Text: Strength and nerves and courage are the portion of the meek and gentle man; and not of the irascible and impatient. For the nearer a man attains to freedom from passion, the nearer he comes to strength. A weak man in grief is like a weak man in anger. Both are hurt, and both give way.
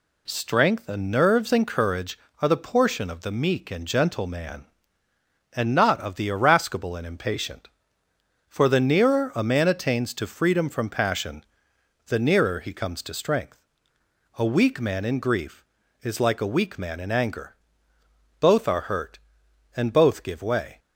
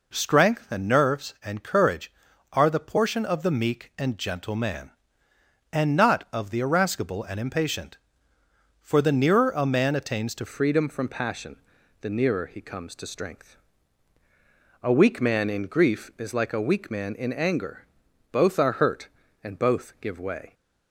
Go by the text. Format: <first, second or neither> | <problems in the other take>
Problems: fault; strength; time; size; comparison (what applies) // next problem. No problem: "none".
first | changes voice at "freedom"; from 10.4 s on; 10.1 s long